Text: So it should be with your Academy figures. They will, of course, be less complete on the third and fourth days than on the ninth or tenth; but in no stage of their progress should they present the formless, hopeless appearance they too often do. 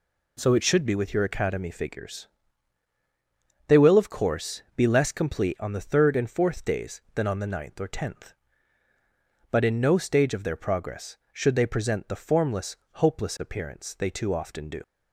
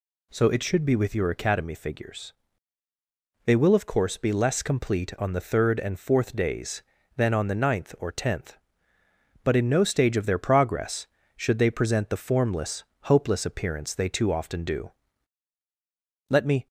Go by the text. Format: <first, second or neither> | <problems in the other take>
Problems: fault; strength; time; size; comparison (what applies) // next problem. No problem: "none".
first | goes on to say "Let me"; slight; from 16.2 s on; 0.38 s long